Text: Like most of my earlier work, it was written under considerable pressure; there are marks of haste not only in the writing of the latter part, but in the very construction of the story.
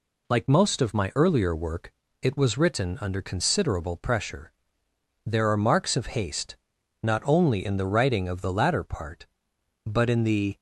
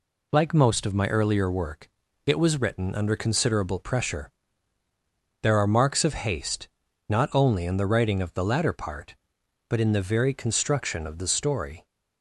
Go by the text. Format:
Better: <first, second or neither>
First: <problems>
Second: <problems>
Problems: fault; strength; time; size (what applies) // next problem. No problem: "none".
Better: second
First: pauses between "haste" and "not"; noticeable; at 6.5 s; 0.46 s long // stops before "very construction of the story"; at 10.5 s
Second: pauses between "haste" and "not"; at 6.6 s; 0.40 s long